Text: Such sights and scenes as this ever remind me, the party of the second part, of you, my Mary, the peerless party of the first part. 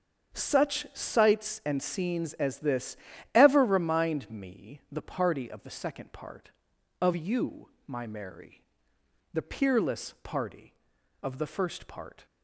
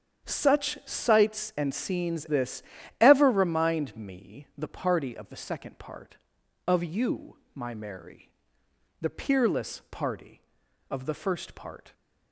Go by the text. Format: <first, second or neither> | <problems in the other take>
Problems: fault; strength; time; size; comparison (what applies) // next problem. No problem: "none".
first | starts louder than the rest; strong; until 1.3 s; 8 dB; also in the first // skips "as"; at 2.2 s // pauses between "this" and "ever"; at 2.6 s; 0.38 s long; also in the first